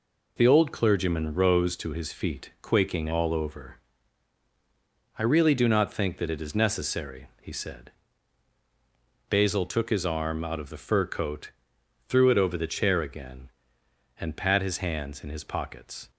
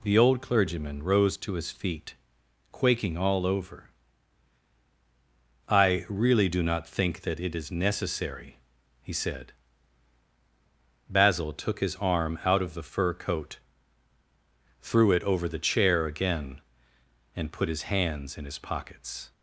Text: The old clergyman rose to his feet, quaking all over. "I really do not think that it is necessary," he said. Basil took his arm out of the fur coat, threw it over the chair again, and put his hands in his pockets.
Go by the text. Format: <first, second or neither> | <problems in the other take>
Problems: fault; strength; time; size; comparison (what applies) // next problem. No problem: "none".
second | says "pat" for "put"; at 14.3 s